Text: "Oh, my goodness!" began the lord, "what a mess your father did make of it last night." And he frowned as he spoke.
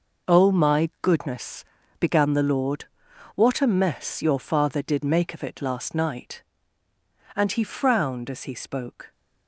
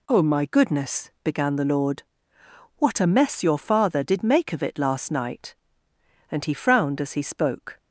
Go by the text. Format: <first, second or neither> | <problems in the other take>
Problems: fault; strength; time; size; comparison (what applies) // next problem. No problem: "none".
second | gets quieter; strong; throughout; 11 dB